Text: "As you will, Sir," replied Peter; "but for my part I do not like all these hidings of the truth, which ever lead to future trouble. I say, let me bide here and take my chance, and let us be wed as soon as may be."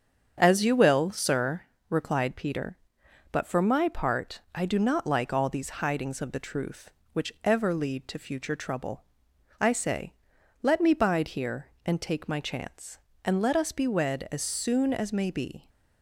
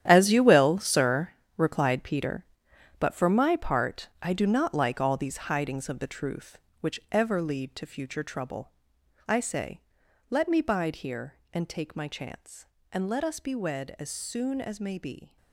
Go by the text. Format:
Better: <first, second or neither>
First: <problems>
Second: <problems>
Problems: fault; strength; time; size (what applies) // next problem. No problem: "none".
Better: first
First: starts louder than the rest; strong; until 1.3 s; 7 dB // pauses between "part" and "I"; slight; at 4.3 s; 0.16 s long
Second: gets quieter; strong; throughout; 13.5 dB // starts louder than the rest; strong; until 1.0 s; 10.5 dB // pauses between "part" and "I"; slight; at 4.0 s; 0.16 s long